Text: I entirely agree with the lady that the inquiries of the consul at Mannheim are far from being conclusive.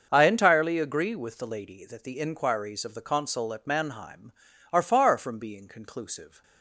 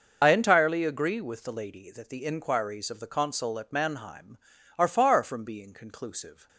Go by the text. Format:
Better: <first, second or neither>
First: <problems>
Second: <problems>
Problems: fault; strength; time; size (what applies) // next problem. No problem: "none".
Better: first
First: starts louder than the rest; until 1.1 s; 6.5 dB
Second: loses the start of "I"; at 0.2 s; 60 ms // starts louder than the rest; until 1.2 s; 6.5 dB